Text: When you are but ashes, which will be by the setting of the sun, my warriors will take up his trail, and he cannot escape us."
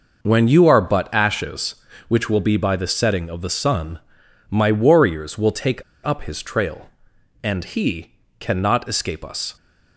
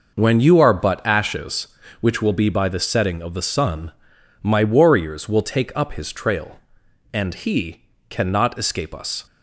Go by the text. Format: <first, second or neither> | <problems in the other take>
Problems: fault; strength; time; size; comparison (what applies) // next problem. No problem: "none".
second | pauses between "take" and "up"; slight; at 5.8 s; 0.22 s long // pauses between "he" and "cannot"; slight; at 8.1 s; 0.26 s long; slight in the second